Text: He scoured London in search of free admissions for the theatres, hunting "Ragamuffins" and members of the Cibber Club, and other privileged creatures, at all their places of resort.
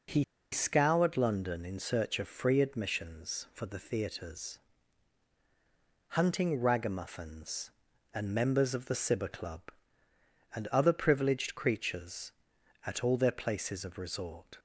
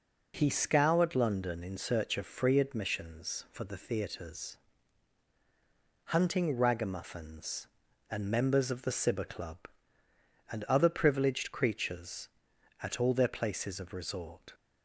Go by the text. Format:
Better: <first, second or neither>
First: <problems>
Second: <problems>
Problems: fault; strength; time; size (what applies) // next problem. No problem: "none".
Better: second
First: pauses between "He" and "scoured"; slight; at 0.2 s; 0.28 s long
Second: none